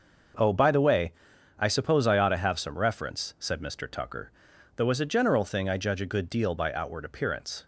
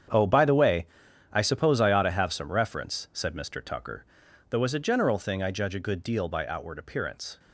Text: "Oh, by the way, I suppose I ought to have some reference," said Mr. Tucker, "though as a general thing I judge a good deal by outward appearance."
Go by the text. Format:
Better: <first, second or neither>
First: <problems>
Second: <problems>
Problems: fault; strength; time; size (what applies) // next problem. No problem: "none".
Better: first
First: starts louder than the rest; until 1.8 s; 6 dB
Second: gets quieter; strong; throughout; 12 dB // starts louder than the rest; strong; until 1.5 s; 8.5 dB